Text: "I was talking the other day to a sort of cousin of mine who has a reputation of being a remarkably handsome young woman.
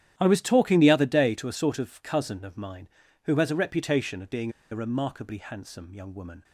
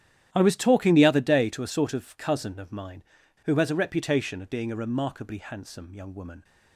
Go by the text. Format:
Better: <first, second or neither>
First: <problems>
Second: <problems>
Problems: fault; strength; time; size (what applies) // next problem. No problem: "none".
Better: second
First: starts louder than the rest; strong; until 1.1 s; 10.5 dB // pauses between "being" and "a"; slight; at 4.4 s; 0.21 s long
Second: starts louder than the rest; strong; until 1.3 s; 11 dB